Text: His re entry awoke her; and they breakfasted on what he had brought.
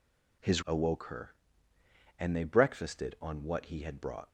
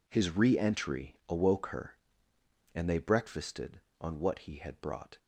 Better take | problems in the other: second | skips "re entry"; at 0.6 s

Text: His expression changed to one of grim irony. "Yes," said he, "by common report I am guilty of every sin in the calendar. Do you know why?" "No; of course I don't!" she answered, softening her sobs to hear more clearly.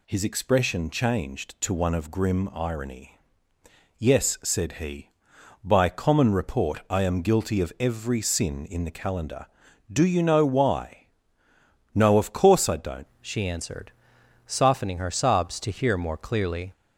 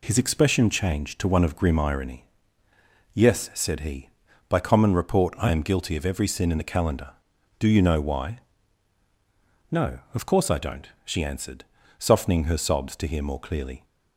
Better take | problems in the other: second | changes voice at "she"; from 13.2 s on; 3.5 s long

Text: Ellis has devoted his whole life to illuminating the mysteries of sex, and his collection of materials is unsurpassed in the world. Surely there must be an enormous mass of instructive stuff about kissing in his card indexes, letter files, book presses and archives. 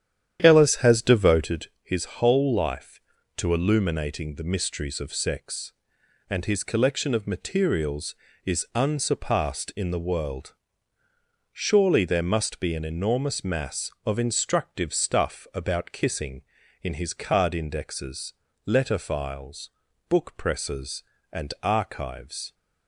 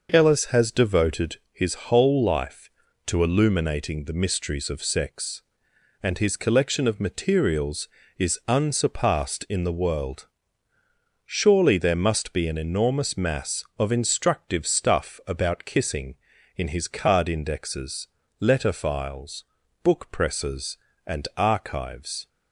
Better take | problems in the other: second | starts louder than the rest; strong; until 1.5 s; 10 dB // pauses between "devoted" and "his"; slight; at 1.6 s; 0.16 s long; slight in the second

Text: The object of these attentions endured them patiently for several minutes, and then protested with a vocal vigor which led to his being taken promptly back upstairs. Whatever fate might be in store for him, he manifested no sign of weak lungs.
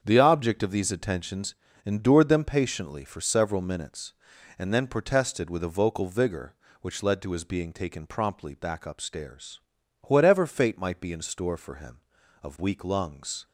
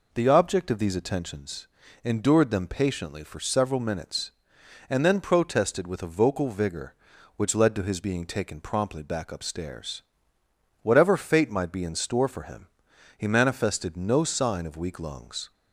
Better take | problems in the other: second | starts louder than the rest; strong; until 1.0 s; 7.5 dB // pauses between "attentions" and "endured"; slight; at 1.5 s; 0.32 s long; slight in the second // skips "he manifested no sign"; at 12.2 s

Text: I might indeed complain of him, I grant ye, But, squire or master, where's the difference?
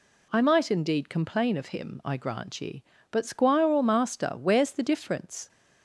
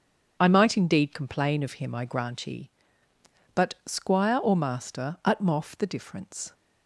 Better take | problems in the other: first | starts louder than the rest; until 1.4 s; 6.5 dB // says "utmoff" for "where's"; at 5.2 s

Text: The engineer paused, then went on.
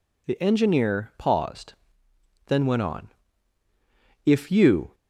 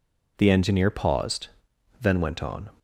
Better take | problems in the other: second | goes on to say "If you"; noticeable; from 4.2 s on; 0.70 s long

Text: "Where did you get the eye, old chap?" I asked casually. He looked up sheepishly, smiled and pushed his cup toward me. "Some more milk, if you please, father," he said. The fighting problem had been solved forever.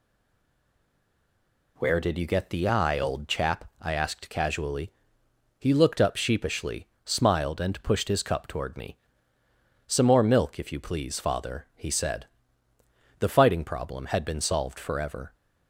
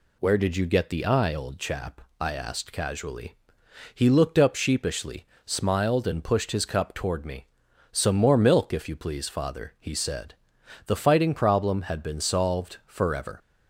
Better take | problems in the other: second | stays silent before the first word; noticeable; until 1.7 s; 1.7 s long

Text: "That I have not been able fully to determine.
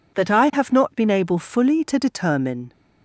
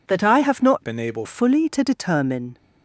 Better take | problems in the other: first | changes voice from "been" to "able"; from 0.8 to 1.2 s; 0.4 s long

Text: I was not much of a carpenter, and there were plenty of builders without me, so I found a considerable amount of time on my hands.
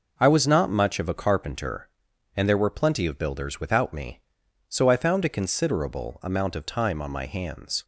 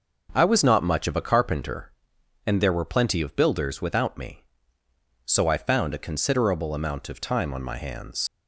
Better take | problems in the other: first | leaves "hands" unfinished; at 8.2 s; 55 ms

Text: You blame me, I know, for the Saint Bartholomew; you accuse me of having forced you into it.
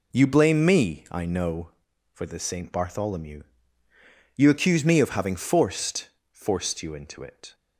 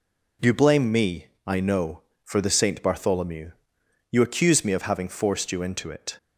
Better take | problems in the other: second | says "forced" twice; at 6.3 s

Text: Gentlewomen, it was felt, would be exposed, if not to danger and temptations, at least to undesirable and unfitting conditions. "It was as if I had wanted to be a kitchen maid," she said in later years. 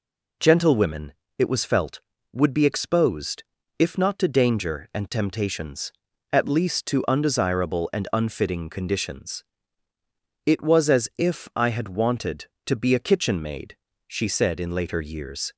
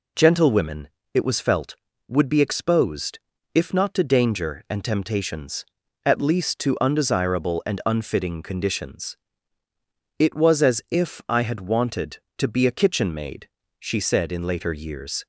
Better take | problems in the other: neither | none

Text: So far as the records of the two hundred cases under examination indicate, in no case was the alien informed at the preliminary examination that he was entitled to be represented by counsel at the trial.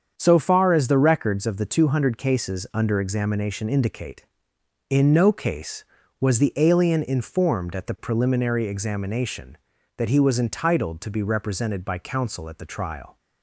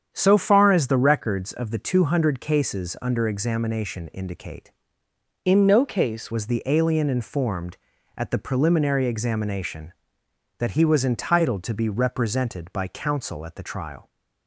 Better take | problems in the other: first | starts louder than the rest; strong; until 1.1 s; 8 dB; strong in the first // changes voice from "in" to "case"; from 5.4 to 6.3 s; 0.9 s long

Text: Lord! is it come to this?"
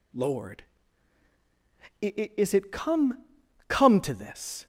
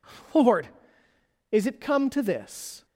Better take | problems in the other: second | says "come" twice; at 3.6 s

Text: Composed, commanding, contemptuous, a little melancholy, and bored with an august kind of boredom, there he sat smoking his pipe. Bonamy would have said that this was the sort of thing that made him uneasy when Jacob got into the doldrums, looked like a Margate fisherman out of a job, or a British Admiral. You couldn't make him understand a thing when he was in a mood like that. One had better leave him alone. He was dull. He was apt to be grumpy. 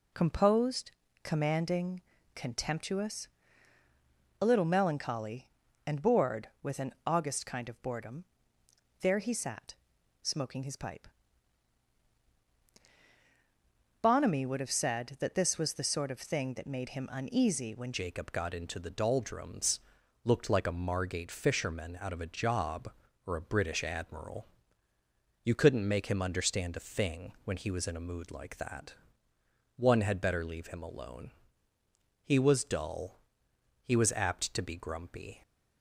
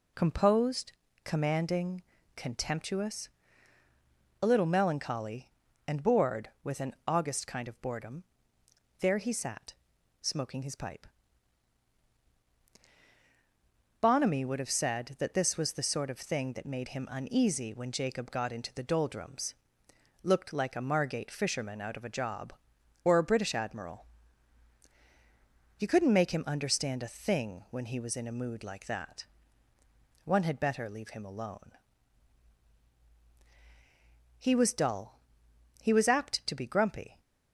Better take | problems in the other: second | pauses between "sat" and "smoking"; noticeable; at 9.7 s; 0.48 s long; noticeable in the second // changes voice at "Jacob"; from 17.9 s on; 17.5 s long

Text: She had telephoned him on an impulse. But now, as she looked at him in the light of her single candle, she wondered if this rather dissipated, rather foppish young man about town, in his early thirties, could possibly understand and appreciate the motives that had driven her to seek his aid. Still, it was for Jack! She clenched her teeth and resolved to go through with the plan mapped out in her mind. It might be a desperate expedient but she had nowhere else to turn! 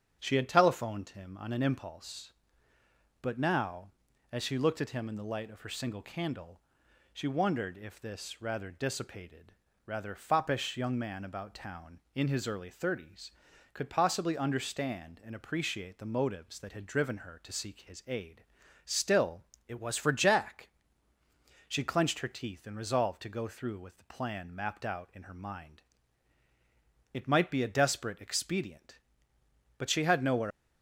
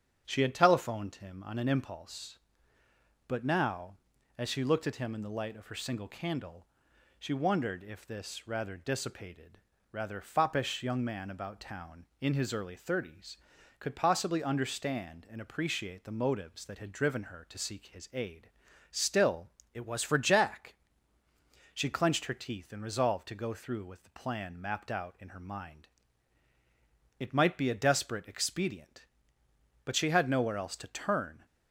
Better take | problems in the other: second | starts louder than the rest; strong; until 1.2 s; 8 dB; strong in the second // stops before "else to turn"; at 30.5 s

